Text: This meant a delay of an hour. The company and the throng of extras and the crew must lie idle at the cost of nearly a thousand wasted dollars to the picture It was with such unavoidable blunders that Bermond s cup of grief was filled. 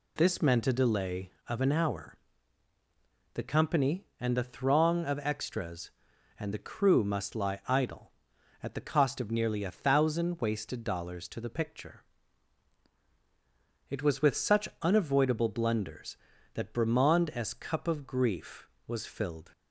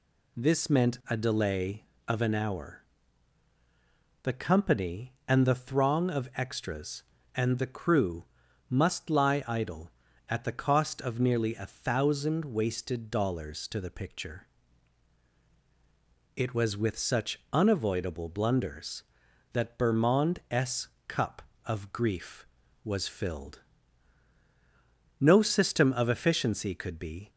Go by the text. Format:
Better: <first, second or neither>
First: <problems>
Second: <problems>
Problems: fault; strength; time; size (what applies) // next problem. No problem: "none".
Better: first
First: pauses between "picture" and "It"; strong; at 12.0 s; 1.8 s long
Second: pauses between "crew" and "must"; at 8.2 s; 0.44 s long // pauses between "picture" and "It"; strong; at 14.4 s; 1.8 s long // pauses between "s" and "cup"; slight; at 20.8 s; 0.18 s long // goes on to say "No system of efficiency could be"; strong; from 25.1 s on; 2.1 s long